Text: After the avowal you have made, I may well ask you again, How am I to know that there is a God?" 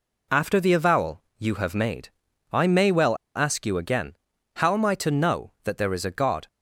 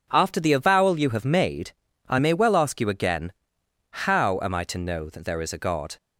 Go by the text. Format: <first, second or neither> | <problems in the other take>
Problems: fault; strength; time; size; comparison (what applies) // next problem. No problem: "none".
second | pauses between "avowal" and "you"; slight; at 1.2 s; 0.16 s long // pauses between "well" and "ask"; slight; at 3.1 s; 0.19 s long